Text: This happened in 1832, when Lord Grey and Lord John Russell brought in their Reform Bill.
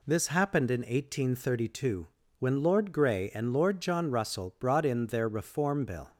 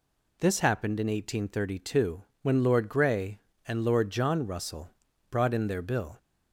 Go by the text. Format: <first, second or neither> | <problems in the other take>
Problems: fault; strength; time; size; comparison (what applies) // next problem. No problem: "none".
first | pauses between "Russell" and "brought"; at 4.8 s; 0.40 s long // skips "Reform"; at 5.8 s